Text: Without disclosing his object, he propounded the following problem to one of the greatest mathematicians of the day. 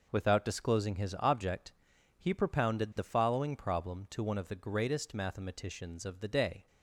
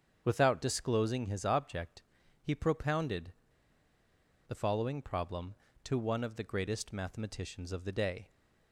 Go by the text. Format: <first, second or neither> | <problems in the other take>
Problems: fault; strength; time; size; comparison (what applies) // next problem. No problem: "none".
first | starts louder than the rest; strong; until 1.2 s; 7.5 dB // pauses between "propounded" and "the"; at 3.3 s; 1.1 s long